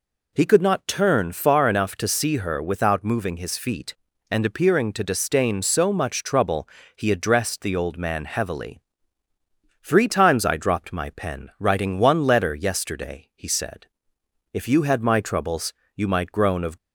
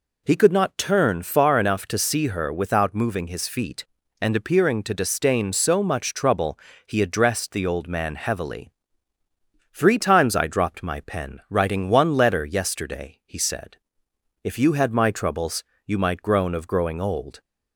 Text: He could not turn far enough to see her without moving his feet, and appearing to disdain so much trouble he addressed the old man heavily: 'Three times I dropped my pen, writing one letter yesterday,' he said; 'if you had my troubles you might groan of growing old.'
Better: second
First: pauses between "trouble" and "he"; slight; at 6.6 s; 0.28 s long // pauses between "troubles" and "you"; slight; at 15.7 s; 0.22 s long // stops before "growing old"; at 16.7 s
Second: pauses between "trouble" and "he"; slight; at 6.5 s; 0.28 s long // pauses between "troubles" and "you"; slight; at 15.6 s; 0.22 s long

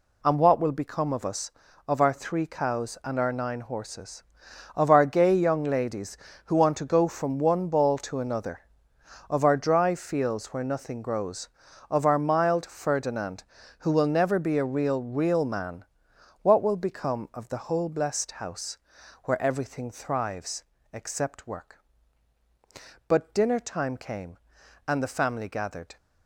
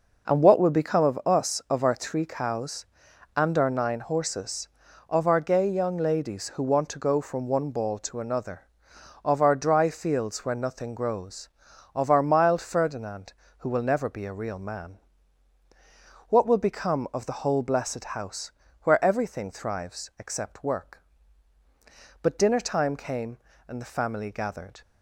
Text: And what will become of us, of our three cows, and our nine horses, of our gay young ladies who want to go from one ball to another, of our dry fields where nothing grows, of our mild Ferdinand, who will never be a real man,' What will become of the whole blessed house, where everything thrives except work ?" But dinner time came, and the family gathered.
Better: second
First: says "real" twice; at 15.0 s // pauses between "thrives" and "except"; slight; at 20.6 s; 0.26 s long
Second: none

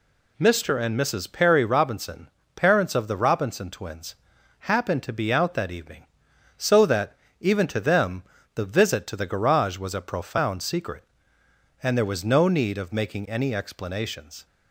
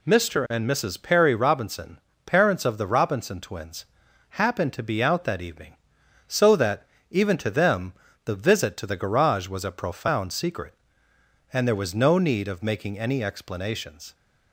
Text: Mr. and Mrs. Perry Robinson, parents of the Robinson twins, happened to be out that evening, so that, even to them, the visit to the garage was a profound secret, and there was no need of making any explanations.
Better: neither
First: none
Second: none

